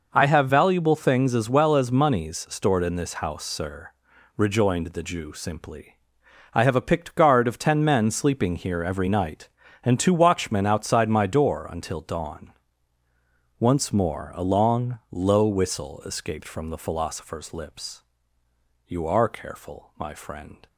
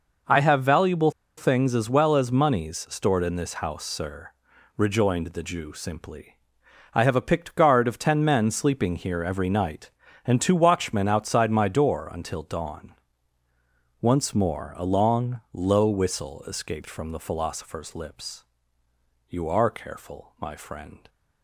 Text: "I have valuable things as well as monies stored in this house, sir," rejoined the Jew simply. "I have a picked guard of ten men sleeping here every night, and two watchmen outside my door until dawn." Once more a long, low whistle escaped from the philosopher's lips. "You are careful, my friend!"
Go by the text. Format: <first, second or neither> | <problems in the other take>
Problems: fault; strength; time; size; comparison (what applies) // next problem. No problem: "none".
first | pauses between "valuable" and "things"; slight; at 1.0 s; 0.27 s long